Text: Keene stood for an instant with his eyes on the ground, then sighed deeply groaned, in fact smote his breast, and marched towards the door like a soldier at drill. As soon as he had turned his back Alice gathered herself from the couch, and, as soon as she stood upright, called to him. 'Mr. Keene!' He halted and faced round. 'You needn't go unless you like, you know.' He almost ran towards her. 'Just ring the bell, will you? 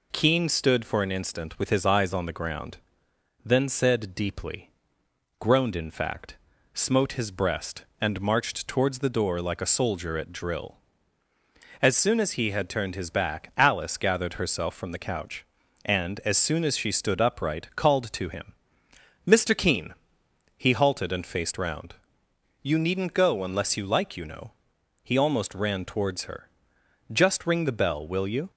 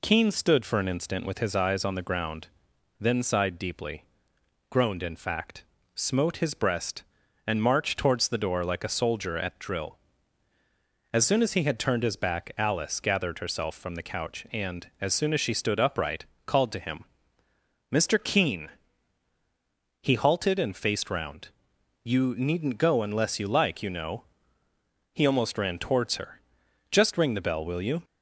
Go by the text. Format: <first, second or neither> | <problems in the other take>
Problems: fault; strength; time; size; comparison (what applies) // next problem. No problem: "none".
second | says "said" for "sighed"; at 3.6 s // pauses between "deeply" and "groaned"; noticeable; at 4.6 s; 0.72 s long; noticeable in the second // pauses between "fact" and "smote"; at 6.3 s; 0.38 s long; slight in the second